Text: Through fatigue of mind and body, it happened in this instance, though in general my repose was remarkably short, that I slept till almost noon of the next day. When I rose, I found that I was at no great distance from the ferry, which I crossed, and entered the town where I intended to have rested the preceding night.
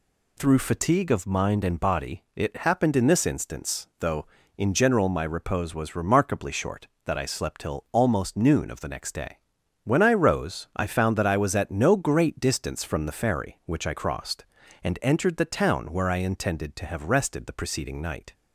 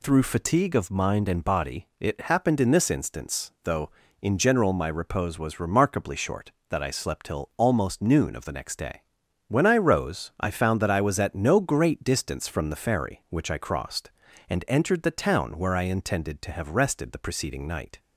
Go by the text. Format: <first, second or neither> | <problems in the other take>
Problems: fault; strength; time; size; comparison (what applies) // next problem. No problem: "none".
neither | none